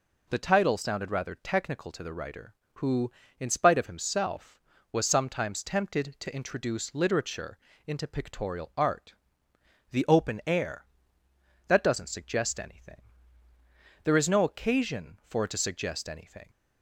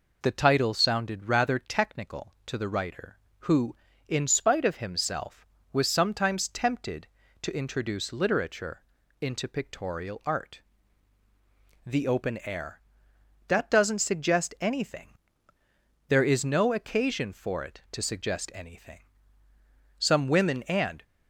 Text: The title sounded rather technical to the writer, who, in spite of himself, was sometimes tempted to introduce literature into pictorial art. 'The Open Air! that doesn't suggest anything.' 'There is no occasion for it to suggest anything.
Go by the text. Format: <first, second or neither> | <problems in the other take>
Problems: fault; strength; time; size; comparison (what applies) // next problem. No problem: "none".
first | pauses between "literature" and "into"; at 8.8 s; 0.38 s long; slight in the first // goes on to say "Some women and"; noticeable; from 19.9 s on; 1.0 s long